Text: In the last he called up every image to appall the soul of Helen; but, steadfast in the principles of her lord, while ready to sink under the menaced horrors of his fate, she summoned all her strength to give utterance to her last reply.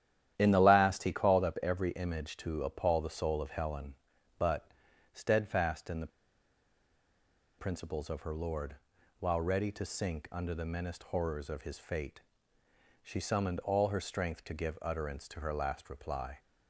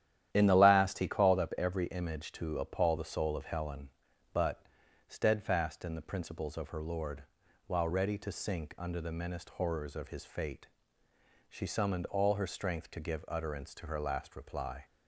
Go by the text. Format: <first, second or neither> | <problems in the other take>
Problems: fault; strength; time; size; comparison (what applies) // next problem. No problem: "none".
second | starts louder than the rest; strong; until 1.3 s; 11 dB; strong in the second // pauses between "the" and "principles"; strong; at 6.1 s; 1.4 s long